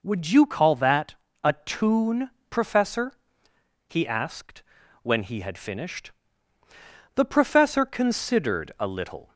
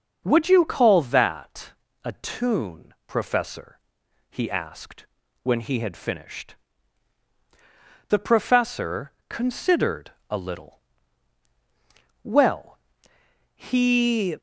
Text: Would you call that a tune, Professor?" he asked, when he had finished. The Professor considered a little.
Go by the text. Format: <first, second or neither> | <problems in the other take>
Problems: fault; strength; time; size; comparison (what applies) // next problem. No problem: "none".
first | starts louder than the rest; until 1.2 s; 6.5 dB // pauses between "that" and "a"; slight; at 1.7 s; 0.34 s long; slight in the first // pauses between "Professor" and "considered"; slight; at 9.1 s; 0.16 s long // pauses between "considered" and "a"; slight; at 10.1 s; 0.16 s long // goes on to say "Well he"; strong; from 12.2 s on; 2.1 s long